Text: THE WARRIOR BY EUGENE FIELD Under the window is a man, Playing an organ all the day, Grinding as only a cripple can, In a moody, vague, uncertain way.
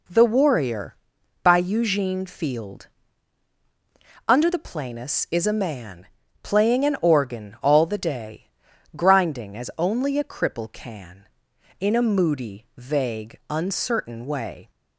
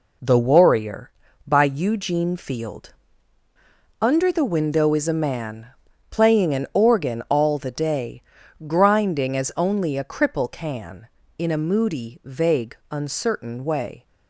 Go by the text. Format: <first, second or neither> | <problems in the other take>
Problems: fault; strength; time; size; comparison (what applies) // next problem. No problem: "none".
second | pauses between "FIELD" and "Under"; strong; at 2.8 s; 1.4 s long; also in the second // says "planus" for "window"; at 4.5 s